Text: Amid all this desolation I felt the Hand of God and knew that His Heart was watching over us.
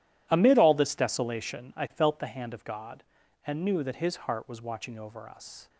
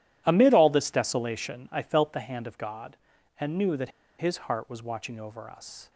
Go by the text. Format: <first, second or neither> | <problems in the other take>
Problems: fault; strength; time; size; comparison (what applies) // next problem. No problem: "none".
first | pauses between "that" and "His"; slight; at 3.9 s; 0.28 s long